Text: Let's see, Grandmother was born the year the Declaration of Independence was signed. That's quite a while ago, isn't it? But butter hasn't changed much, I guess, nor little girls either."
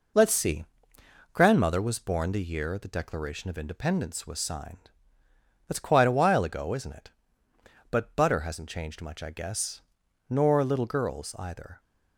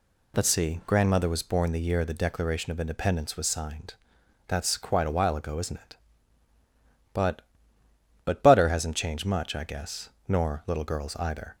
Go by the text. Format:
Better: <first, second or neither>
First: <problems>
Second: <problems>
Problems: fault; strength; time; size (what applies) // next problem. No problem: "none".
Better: first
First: none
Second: says "But" twice; at 8.2 s